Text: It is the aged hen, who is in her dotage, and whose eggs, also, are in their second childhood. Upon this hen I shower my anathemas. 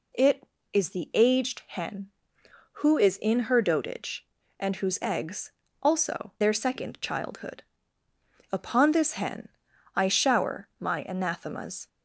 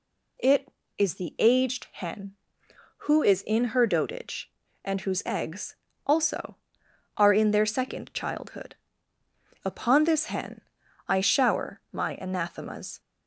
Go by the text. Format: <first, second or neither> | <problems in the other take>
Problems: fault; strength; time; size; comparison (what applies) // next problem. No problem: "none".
second | skips "are in"; at 6.3 s // pauses between "hen" and "I"; noticeable; at 9.4 s; 0.48 s long; noticeable in the second